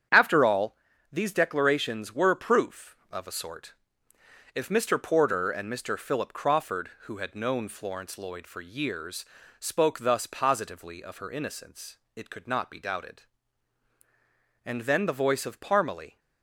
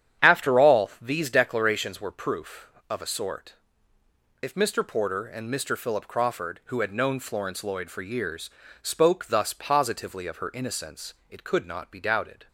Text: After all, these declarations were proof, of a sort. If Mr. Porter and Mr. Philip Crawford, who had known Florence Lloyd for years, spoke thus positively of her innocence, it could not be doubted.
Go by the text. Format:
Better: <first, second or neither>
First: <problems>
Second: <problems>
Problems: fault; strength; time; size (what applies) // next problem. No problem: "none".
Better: second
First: starts louder than the rest; strong; until 1.4 s; 8.5 dB // goes on to say "And then the voice of Parmalee"; from 14.6 s on; 1.5 s long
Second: starts louder than the rest; strong; until 1.3 s; 9 dB